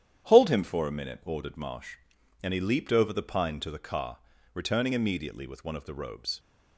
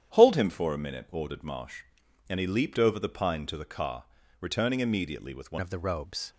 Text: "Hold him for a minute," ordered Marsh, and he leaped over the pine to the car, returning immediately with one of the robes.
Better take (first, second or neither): first